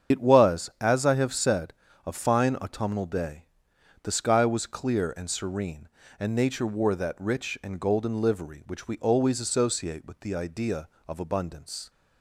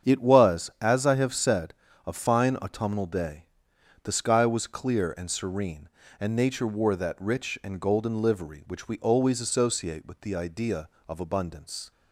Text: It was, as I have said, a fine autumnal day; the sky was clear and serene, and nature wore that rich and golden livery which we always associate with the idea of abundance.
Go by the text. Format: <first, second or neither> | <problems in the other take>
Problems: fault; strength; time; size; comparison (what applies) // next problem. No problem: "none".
second | loses the start of "It"; at 0.1 s; 65 ms // starts louder than the rest; strong; until 1.2 s; 8 dB; strong in the second